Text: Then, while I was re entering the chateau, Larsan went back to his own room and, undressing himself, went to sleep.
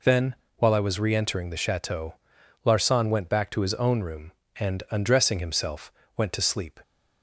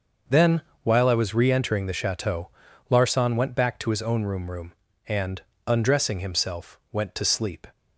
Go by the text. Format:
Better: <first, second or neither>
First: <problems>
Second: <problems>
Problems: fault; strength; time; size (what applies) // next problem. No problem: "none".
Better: first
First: none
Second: starts louder than the rest; until 1.5 s; 6.5 dB // says "room" twice; at 4.5 s